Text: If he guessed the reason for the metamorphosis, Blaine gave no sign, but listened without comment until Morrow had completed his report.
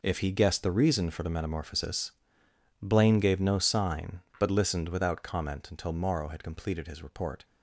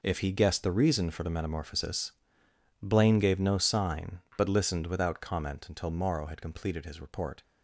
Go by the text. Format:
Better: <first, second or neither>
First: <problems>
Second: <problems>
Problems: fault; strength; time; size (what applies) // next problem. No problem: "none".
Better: neither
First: none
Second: none